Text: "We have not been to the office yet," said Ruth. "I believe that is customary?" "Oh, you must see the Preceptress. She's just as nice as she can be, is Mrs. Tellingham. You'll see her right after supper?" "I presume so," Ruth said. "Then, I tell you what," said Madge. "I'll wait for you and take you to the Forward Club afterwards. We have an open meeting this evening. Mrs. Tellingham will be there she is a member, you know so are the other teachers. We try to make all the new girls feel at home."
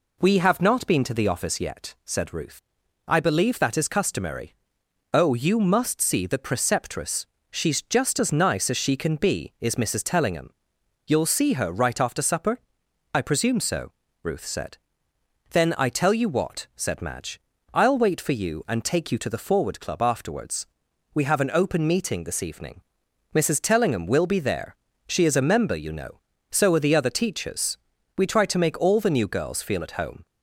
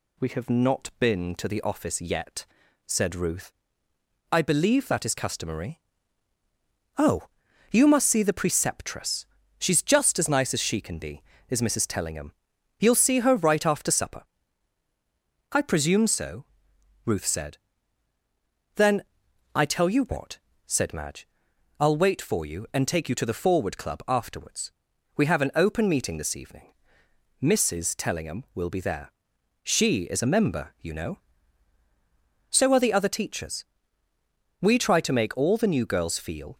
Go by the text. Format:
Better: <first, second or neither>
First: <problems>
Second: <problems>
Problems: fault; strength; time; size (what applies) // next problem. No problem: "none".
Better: first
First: pauses between "there" and "she"; slight; at 24.7 s; 0.32 s long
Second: pauses between "there" and "she"; noticeable; at 29.1 s; 0.58 s long // stops before "at home"; at 36.5 s